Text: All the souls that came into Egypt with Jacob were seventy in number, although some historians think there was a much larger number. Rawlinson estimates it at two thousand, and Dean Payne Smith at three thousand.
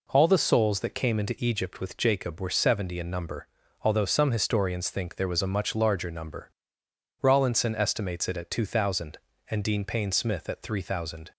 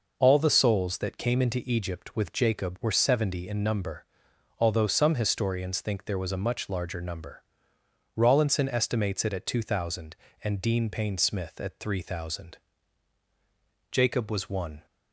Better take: first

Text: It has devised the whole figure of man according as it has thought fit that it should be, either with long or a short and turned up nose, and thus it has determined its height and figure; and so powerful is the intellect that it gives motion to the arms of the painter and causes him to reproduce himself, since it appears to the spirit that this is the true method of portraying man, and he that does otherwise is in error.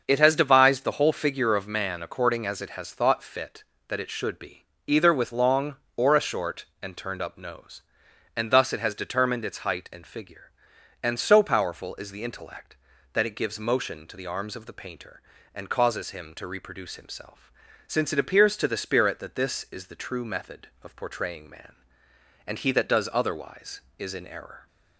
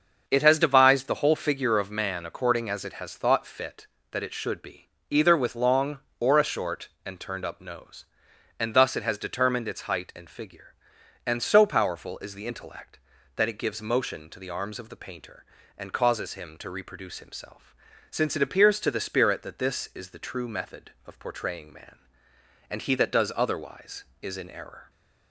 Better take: neither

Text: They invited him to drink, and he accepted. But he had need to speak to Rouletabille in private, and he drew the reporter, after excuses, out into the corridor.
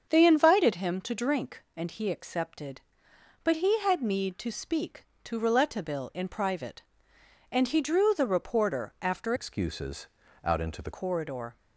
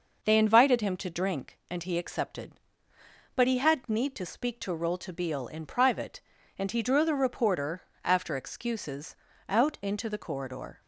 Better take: second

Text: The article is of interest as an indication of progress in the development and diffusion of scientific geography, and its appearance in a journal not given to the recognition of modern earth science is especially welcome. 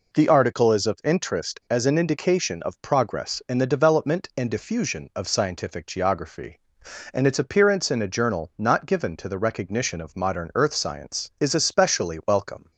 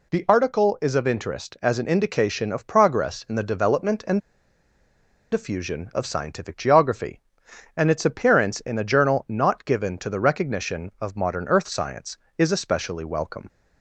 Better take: first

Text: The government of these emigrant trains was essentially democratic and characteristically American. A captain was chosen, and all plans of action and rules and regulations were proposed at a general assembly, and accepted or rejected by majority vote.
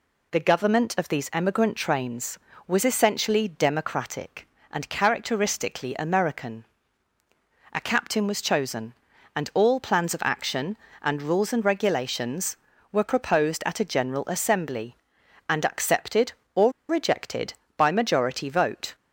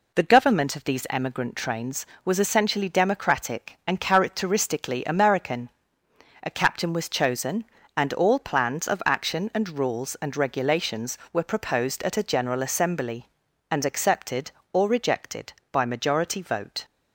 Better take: second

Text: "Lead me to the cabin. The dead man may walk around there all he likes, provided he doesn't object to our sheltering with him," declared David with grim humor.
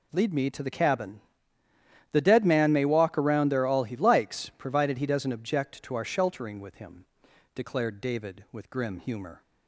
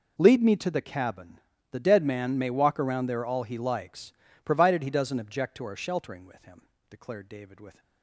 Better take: first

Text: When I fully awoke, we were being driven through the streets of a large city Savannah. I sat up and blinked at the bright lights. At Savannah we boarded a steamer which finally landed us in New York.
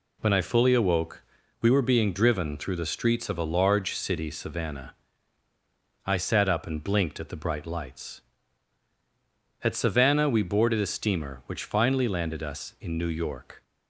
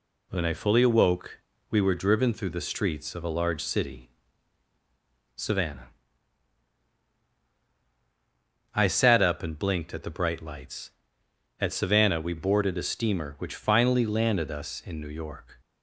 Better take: first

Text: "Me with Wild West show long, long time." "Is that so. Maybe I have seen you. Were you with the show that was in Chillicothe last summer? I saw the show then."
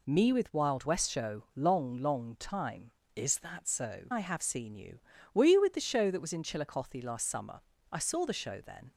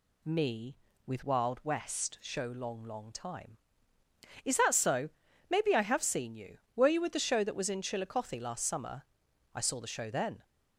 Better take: second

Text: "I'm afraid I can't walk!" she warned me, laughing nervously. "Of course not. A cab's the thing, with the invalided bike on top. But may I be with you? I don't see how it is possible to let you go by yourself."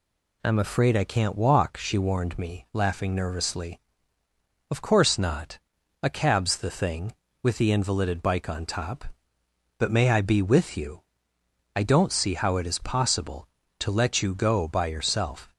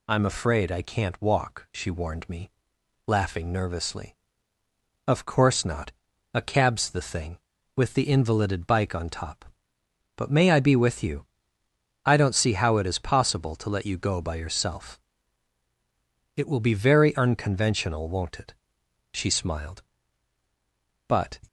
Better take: first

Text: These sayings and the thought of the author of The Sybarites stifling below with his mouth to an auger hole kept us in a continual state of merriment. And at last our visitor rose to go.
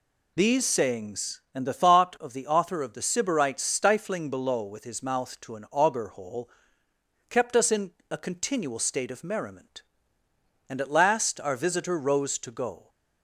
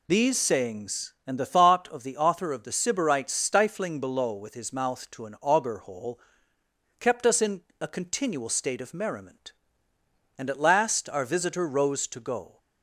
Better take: neither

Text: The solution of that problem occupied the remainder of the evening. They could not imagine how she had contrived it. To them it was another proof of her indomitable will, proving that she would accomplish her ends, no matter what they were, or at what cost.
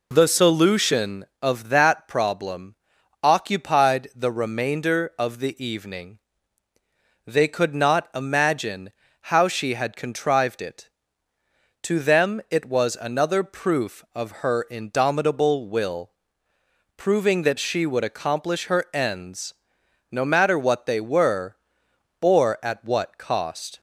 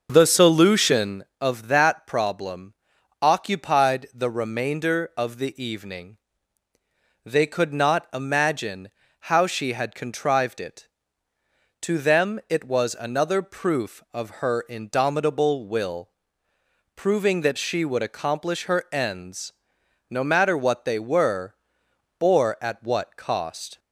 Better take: first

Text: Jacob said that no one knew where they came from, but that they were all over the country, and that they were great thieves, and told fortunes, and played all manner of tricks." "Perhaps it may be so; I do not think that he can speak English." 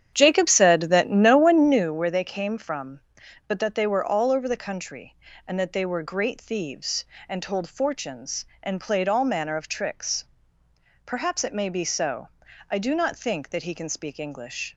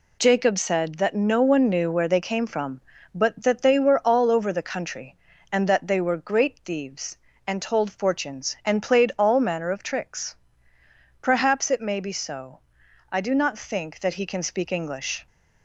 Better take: second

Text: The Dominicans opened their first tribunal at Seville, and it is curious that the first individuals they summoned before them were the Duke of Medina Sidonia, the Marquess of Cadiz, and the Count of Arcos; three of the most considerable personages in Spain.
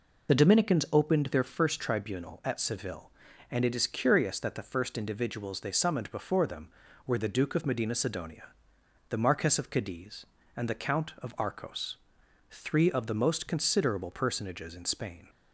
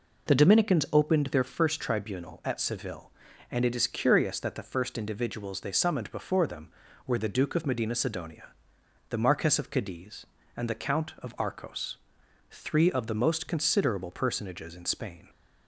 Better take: second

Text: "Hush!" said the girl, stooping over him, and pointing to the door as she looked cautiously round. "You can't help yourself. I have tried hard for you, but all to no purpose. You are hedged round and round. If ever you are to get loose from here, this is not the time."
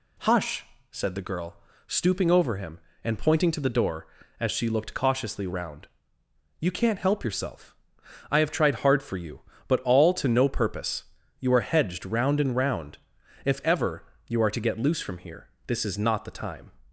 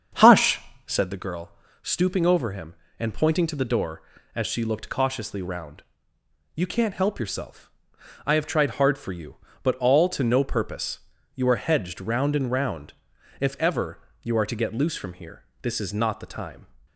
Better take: first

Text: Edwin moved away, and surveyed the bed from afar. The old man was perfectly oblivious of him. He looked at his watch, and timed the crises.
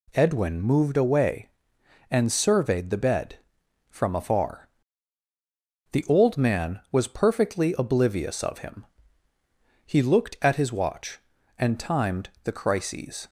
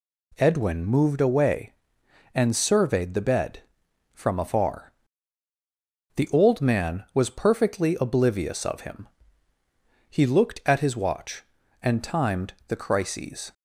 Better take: neither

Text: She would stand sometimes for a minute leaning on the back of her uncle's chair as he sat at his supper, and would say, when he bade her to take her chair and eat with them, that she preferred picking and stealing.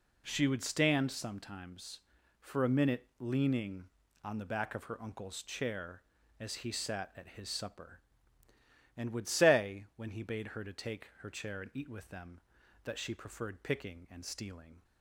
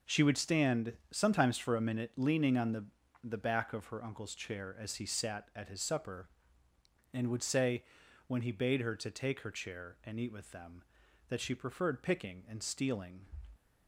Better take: first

